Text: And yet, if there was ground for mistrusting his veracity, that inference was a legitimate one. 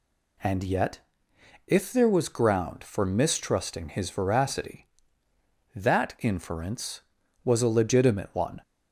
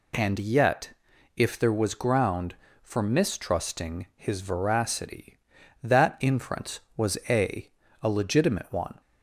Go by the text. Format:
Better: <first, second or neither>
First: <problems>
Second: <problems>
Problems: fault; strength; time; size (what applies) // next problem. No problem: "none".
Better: first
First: none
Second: says "a" twice; at 8.0 s